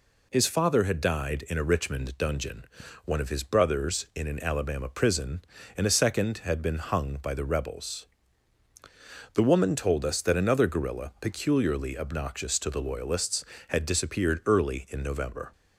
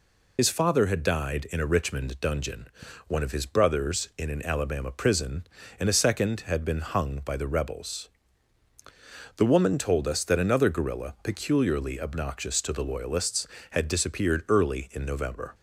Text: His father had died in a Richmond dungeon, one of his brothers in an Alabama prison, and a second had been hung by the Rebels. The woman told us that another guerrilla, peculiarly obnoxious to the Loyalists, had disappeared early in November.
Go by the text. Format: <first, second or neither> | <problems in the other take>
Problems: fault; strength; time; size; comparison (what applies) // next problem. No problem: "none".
first | loses the start of "His"; at 0.3 s; 65 ms